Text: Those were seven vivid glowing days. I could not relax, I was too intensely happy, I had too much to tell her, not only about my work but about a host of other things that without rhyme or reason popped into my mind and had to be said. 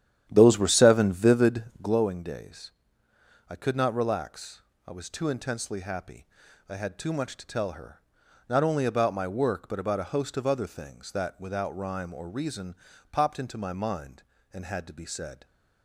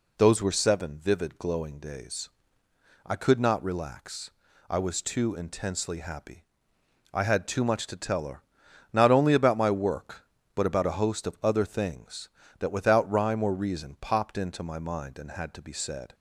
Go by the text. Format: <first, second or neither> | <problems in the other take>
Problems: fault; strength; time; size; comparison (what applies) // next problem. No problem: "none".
second | starts louder than the rest; strong; until 2.1 s; 10.5 dB // pauses between "vivid" and "glowing"; slight; at 1.6 s; 0.18 s long // pauses between "reason" and "popped"; at 12.7 s; 0.38 s long